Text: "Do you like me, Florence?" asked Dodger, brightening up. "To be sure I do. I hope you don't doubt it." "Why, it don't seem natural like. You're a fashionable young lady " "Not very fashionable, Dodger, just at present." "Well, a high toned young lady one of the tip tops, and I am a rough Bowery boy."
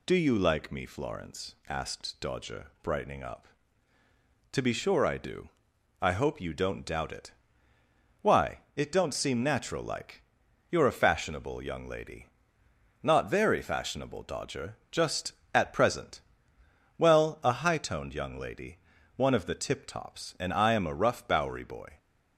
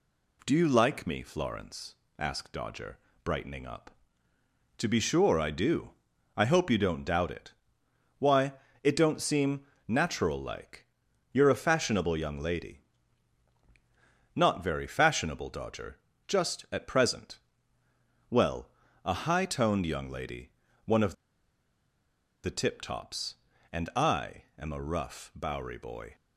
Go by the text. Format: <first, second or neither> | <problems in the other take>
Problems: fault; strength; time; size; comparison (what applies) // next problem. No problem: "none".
first | pauses between "seem" and "natural"; slight; at 9.6 s; 0.20 s long // pauses between "lady" and "one"; slight; at 20.5 s; 0.34 s long; also in the first // pauses between "of" and "the"; strong; at 21.1 s; 1.3 s long